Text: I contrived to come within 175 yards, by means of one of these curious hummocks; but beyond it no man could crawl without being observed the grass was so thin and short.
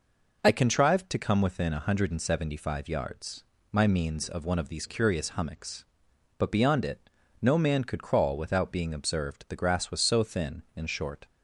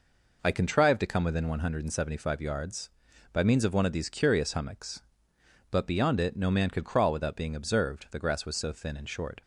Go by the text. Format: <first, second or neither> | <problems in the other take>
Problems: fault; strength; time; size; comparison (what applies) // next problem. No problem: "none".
second | says "my" for "by"; at 3.7 s // pauses between "it" and "no"; slight; at 7.0 s; 0.32 s long